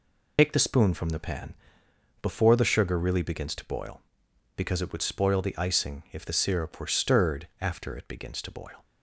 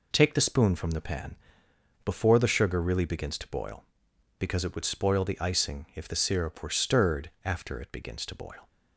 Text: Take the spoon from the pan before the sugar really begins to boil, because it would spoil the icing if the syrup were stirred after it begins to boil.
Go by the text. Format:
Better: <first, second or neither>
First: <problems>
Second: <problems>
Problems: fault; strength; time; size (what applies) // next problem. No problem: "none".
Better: second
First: loses the start of "Take"; at 0.3 s; 85 ms // pauses between "pan" and "before"; noticeable; at 1.5 s; 0.68 s long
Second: pauses between "pan" and "before"; noticeable; at 1.3 s; 0.69 s long